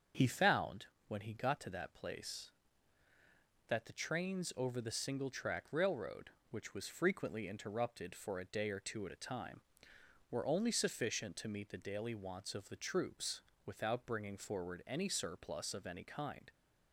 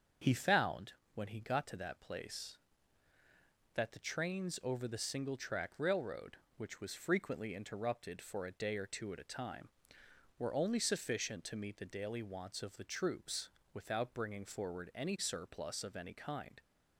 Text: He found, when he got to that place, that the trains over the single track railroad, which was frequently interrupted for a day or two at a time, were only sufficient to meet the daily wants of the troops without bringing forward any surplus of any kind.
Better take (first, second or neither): neither